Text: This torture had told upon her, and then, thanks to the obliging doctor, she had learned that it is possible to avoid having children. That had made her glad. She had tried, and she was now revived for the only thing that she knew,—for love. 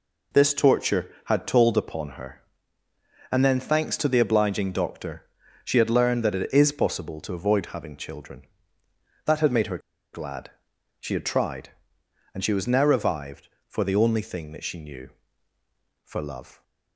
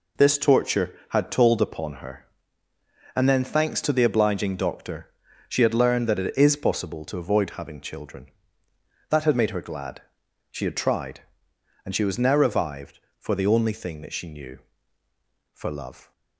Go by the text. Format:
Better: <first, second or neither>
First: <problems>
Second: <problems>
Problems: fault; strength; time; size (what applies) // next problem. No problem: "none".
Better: second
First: pauses between "her" and "glad"; slight; at 9.7 s; 0.35 s long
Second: none